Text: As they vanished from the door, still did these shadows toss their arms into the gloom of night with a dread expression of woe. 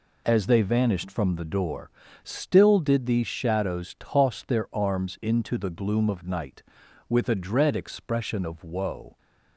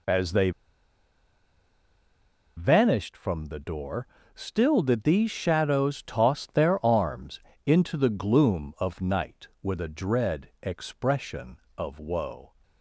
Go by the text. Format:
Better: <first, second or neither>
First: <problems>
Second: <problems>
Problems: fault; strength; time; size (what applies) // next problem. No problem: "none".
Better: first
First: none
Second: pauses between "they" and "vanished"; strong; at 0.5 s; 2.0 s long // pauses between "arms" and "into"; slight; at 7.3 s; 0.26 s long